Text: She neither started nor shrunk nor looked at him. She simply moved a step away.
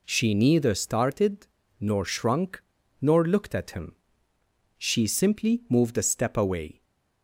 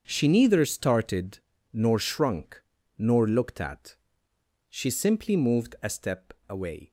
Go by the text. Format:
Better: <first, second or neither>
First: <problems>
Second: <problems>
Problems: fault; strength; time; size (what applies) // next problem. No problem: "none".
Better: first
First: pauses between "started" and "nor"; slight; at 1.4 s; 0.32 s long // pauses between "shrunk" and "nor"; at 2.6 s; 0.38 s long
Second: starts louder than the rest; until 1.0 s; 7 dB // pauses between "started" and "nor"; slight; at 1.3 s; 0.34 s long // pauses between "shrunk" and "nor"; at 2.6 s; 0.38 s long // skips "him"; at 4.3 s